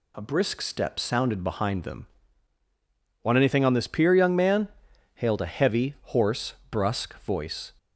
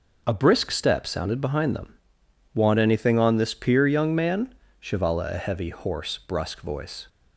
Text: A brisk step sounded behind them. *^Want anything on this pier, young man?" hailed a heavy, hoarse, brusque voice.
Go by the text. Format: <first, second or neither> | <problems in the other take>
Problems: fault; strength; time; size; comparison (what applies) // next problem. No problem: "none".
first | says "shivala" for "hailed"; at 4.8 s